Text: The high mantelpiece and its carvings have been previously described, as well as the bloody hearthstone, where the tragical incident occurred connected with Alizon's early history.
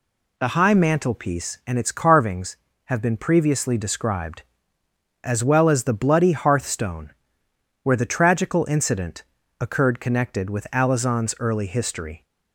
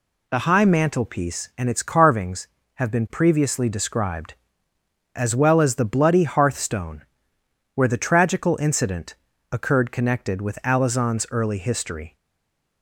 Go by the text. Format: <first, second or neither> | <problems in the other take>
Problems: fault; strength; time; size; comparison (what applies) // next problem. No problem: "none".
first | pauses between "incident" and "occurred"; slight; at 9.1 s; 0.36 s long; slight in the first // stays silent after the last word; slight; from 12.1 s on; 0.7 s long